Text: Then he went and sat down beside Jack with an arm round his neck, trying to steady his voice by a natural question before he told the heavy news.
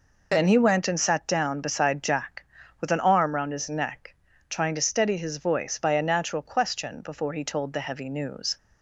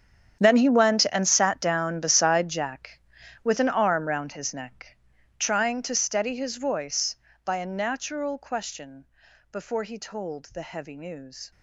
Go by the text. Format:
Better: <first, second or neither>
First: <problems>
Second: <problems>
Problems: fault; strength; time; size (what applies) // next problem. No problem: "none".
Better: first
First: none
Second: gets quieter; strong; throughout; 16.5 dB // pauses between "question" and "before"; noticeable; at 9.0 s; 0.46 s long